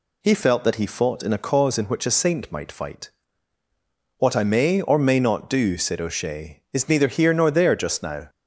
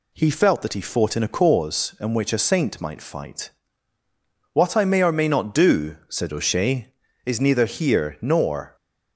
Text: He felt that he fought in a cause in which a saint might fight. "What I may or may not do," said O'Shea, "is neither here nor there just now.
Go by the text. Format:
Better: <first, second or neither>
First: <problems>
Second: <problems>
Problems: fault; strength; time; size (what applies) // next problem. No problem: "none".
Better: first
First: none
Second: stops before "there just now"; at 8.7 s